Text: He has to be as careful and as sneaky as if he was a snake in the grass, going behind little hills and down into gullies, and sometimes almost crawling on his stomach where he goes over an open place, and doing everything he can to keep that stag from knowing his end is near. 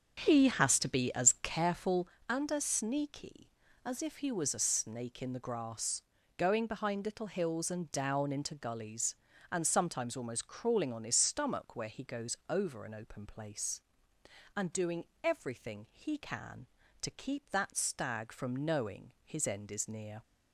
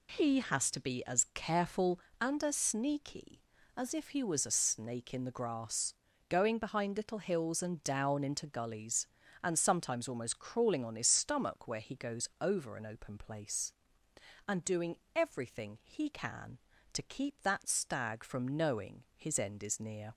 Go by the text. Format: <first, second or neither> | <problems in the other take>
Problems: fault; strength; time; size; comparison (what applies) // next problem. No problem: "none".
second | starts louder than the rest; until 1.6 s; 7 dB // pauses between "doing" and "everything"; slight; at 15.0 s; 0.18 s long; slight in the second